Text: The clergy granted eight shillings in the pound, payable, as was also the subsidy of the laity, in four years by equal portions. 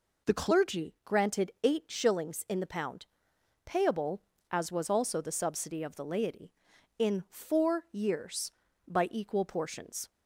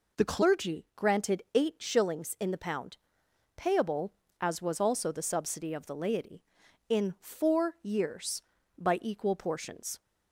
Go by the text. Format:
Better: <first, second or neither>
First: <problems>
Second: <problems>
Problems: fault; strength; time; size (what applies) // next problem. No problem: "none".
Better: neither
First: none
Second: none